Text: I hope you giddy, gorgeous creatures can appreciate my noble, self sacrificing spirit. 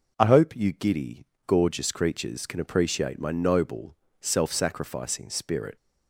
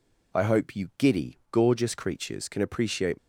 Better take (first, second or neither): first